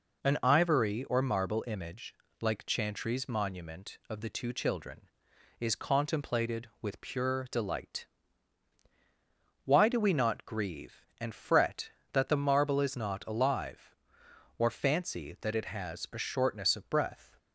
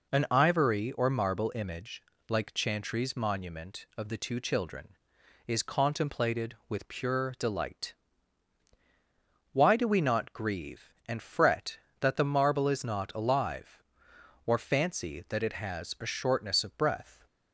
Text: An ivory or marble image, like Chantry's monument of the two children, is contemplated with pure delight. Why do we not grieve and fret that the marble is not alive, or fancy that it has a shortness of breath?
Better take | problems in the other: neither | none

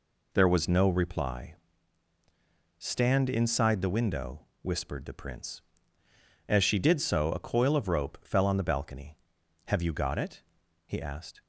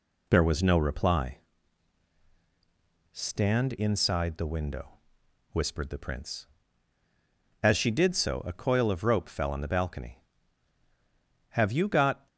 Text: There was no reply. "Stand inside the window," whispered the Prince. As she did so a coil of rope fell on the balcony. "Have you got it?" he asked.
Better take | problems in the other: first | stops before "it he asked"; at 12.2 s

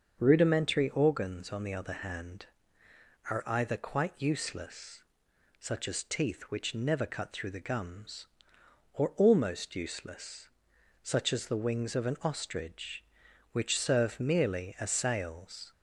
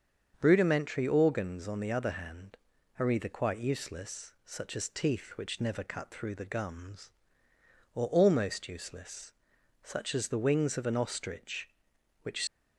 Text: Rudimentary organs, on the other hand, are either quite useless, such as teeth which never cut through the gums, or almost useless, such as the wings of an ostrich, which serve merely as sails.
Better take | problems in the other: first | starts louder than the rest; strong; until 1.4 s; 7 dB; also in the first // stops before "serve merely as sails"; at 12.4 s

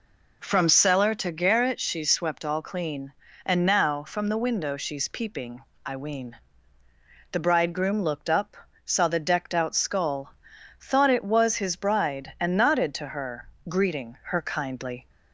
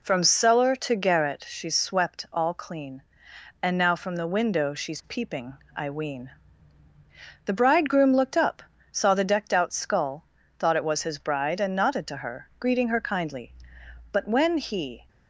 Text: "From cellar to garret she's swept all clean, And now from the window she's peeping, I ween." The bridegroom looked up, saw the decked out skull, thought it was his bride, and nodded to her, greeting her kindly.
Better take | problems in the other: first | goes on to say "But when he"; noticeable; from 14.1 s on; 0.96 s long

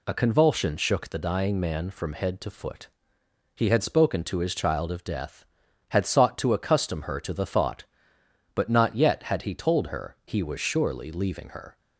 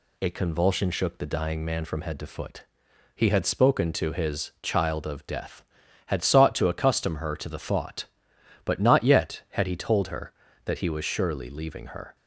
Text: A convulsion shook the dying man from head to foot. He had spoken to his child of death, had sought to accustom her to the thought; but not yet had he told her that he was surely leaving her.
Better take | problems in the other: second | skips "that"; at 10.2 s

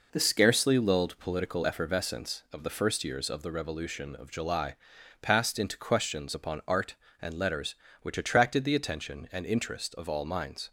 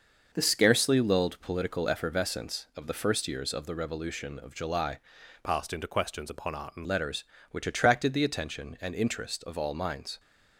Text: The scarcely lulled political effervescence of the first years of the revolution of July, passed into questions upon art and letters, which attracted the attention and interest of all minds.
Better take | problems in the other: first | changes voice from "passed" to "and"; from 5.4 to 6.8 s; 1.4 s long

